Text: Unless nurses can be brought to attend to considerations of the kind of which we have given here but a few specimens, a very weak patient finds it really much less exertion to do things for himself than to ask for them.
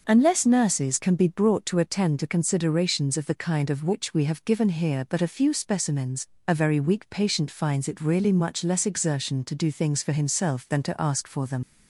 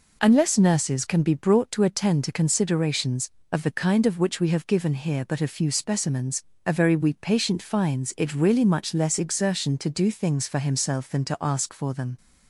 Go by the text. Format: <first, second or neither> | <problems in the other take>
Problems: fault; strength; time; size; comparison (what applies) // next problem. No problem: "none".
second | starts louder than the rest; noticeable; until 1.0 s; 6 dB // leaves "them" unfinished; at 11.6 s; 90 ms